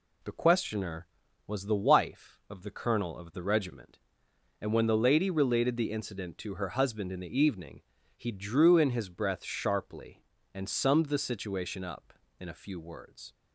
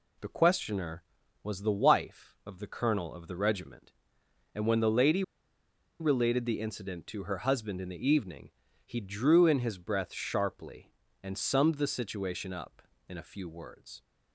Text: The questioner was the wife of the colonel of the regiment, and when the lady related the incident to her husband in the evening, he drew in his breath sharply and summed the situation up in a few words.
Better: first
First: none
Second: pauses between "lady" and "related"; noticeable; at 5.2 s; 0.78 s long

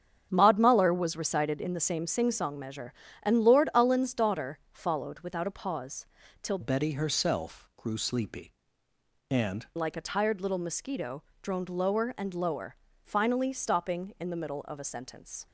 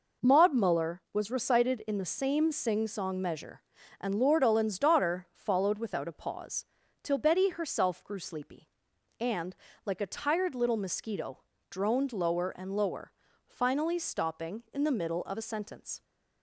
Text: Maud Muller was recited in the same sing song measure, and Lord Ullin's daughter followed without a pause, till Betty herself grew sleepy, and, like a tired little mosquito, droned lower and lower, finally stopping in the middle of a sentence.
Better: second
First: starts louder than the rest; strong; until 1.3 s; 8 dB // changes voice from "Betty" to "and"; from 6.6 to 9.6 s; 3.0 s long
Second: none

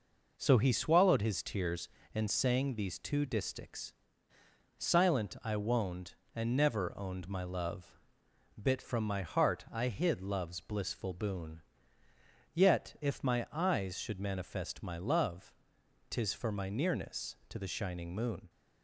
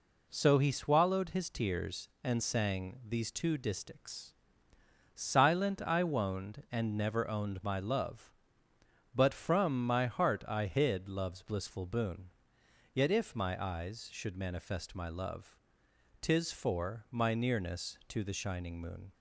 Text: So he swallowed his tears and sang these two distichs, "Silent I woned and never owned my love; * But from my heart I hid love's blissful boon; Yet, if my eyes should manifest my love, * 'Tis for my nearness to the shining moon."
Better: second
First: says "Bit" for "But"; at 8.6 s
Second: none

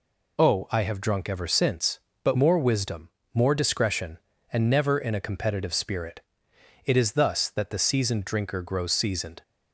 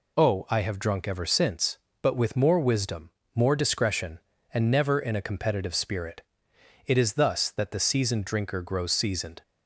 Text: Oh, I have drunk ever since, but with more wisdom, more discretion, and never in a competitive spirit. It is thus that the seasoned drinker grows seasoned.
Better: second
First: skips "with"; at 2.3 s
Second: none

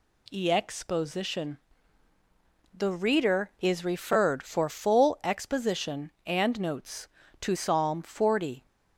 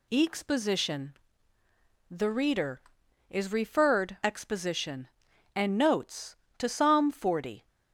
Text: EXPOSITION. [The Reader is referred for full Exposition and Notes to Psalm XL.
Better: first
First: none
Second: skips "for full"; at 4.1 s

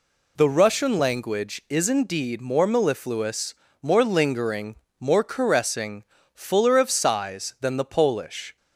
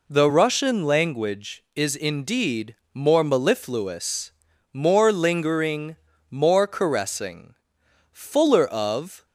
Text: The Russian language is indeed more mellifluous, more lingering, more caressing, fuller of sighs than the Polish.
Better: first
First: none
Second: pauses between "indeed" and "more"; slight; at 2.7 s; 0.18 s long // stops before "sighs than the Polish"; at 9.2 s

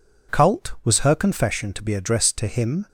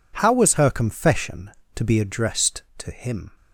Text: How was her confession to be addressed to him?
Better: second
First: says "Cult" for "How"; at 0.3 s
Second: none

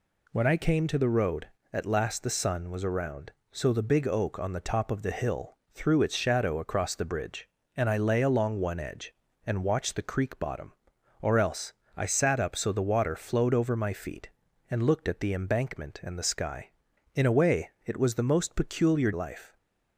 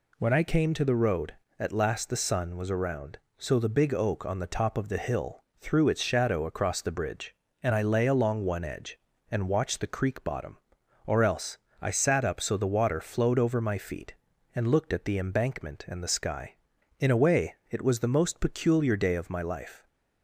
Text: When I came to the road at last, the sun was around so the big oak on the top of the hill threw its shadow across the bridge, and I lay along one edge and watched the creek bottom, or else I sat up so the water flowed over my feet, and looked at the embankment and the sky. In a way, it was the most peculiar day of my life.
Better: second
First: pauses between "hill" and "threw"; slight; at 5.5 s; 0.16 s long // pauses between "else" and "I"; slight; at 11.7 s; 0.24 s long // skips "day of my"; at 19.1 s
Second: pauses between "hill" and "threw"; slight; at 5.4 s; 0.16 s long // pauses between "else" and "I"; slight; at 11.5 s; 0.24 s long

